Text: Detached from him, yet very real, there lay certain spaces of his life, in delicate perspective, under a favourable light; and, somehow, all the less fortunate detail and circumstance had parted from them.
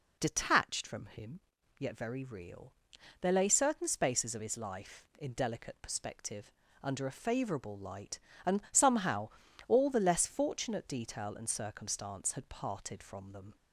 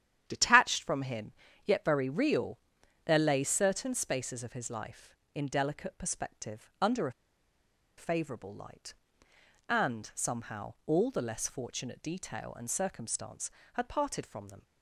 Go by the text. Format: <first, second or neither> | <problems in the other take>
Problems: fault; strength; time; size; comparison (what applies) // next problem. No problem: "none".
first | starts louder than the rest; strong; until 1.2 s; 10 dB // pauses between "a" and "favourable"; noticeable; at 7.1 s; 0.85 s long